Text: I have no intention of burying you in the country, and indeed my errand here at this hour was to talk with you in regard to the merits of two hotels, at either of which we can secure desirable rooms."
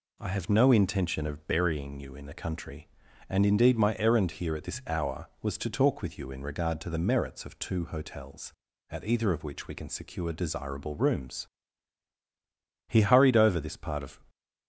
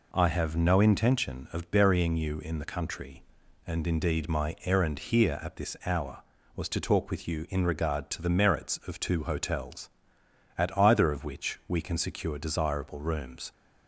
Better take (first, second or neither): second